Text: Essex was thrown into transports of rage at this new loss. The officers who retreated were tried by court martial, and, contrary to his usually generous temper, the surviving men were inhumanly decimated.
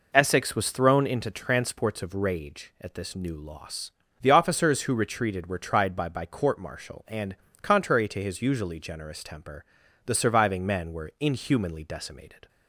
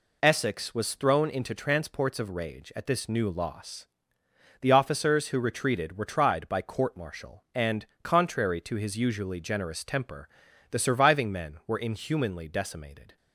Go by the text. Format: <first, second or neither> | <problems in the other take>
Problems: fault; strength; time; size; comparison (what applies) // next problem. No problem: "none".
second | says "by" twice; at 6.0 s